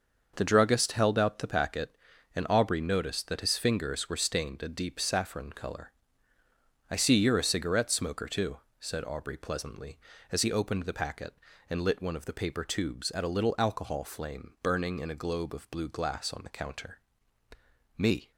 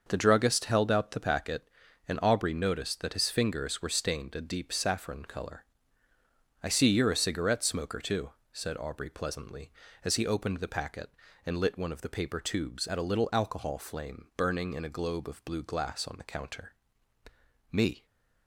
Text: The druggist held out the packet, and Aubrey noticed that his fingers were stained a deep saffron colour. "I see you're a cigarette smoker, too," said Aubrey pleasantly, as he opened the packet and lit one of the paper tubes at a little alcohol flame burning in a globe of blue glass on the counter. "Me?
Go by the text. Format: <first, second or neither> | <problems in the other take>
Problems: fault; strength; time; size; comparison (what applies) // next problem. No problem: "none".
neither | starts louder than the rest; the same in both